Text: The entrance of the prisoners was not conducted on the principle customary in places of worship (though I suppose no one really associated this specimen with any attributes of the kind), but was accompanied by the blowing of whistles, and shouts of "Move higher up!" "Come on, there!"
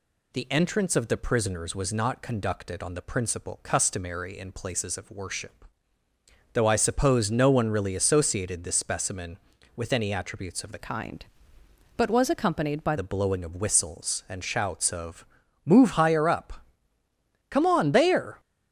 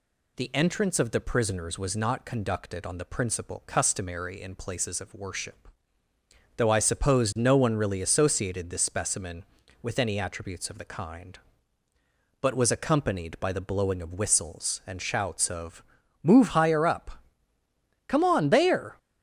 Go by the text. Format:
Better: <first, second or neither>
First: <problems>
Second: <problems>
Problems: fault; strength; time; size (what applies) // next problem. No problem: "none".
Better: second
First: changes voice from "kind" to "by"; from 10.7 to 12.9 s; 2.2 s long // pauses between "of" and "Move"; at 15.2 s; 0.40 s long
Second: pauses between "of" and "Move"; at 15.8 s; 0.40 s long